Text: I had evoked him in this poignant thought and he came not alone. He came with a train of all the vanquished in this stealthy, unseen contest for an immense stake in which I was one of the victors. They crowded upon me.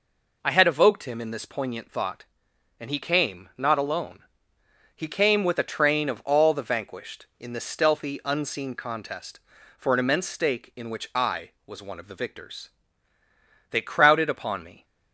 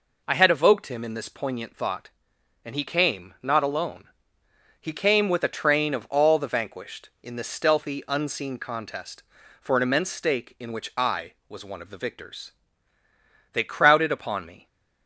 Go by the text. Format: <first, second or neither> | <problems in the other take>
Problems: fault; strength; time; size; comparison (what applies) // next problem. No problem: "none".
neither | none